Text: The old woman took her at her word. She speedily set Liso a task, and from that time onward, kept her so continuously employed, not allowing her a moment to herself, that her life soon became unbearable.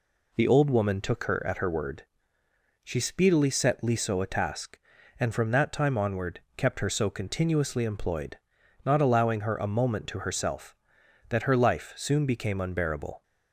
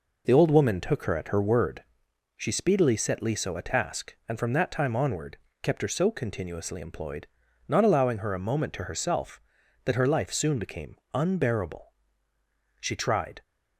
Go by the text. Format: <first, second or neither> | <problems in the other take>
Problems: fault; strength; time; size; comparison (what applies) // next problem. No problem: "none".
first | pauses between "became" and "unbearable"; slight; at 10.9 s; 0.18 s long // goes on to say "She tried"; noticeable; from 12.7 s on; 0.62 s long